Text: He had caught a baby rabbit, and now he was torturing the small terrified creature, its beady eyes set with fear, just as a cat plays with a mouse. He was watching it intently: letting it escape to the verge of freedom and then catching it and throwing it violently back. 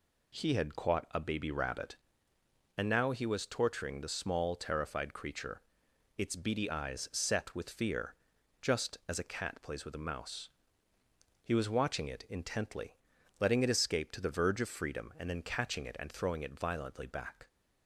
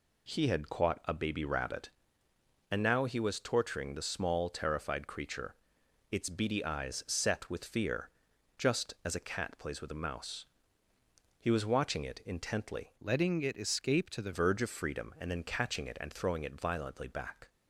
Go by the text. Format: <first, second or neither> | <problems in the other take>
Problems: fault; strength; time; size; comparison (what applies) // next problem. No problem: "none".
first | changes voice from "letting" to "the"; from 13.0 to 14.3 s; 1.3 s long